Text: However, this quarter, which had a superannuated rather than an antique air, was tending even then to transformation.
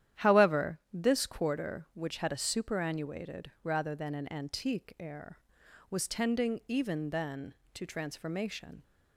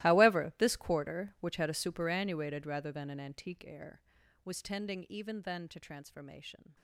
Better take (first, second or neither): first